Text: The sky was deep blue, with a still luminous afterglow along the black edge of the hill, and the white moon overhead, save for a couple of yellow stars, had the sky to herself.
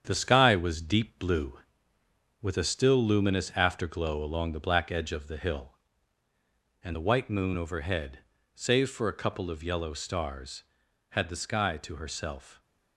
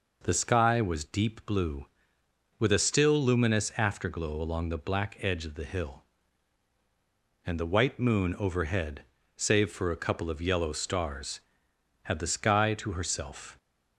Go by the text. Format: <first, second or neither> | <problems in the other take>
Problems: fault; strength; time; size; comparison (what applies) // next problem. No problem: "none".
second | gets quieter; noticeable; throughout; 5 dB